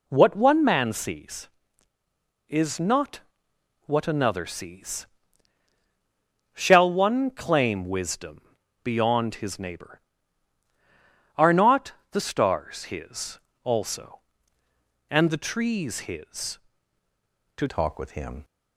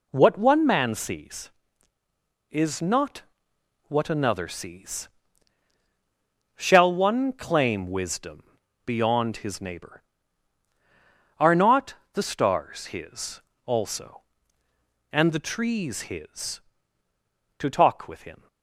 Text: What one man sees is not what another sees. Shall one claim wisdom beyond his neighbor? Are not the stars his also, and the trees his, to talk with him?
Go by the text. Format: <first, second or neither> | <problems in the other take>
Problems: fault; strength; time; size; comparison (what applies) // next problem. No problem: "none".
second | pauses between "not" and "what"; noticeable; at 3.1 s; 0.68 s long; noticeable in the second // pauses between "wisdom" and "beyond"; at 8.4 s; 0.44 s long; also in the second // pauses between "not" and "the"; slight; at 11.9 s; 0.22 s long; slight in the second // pauses between "his" and "also"; slight; at 13.4 s; 0.24 s long; slight in the second // changes voice at "talk"; from 17.6 s on; 0.8 s long